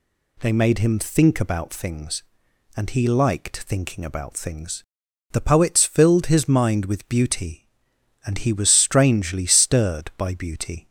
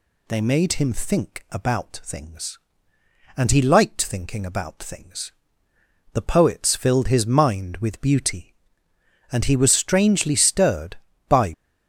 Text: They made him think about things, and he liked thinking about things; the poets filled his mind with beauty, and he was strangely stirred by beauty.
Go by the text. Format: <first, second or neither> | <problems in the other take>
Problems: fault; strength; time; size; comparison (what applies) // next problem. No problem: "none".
first | stops before "beauty"; at 11.5 s